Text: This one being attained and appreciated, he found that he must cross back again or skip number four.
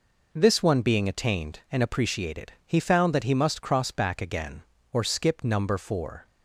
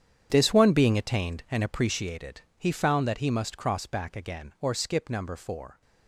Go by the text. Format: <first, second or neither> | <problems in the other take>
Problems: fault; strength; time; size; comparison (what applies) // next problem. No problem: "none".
first | gets quieter; strong; throughout; 14.5 dB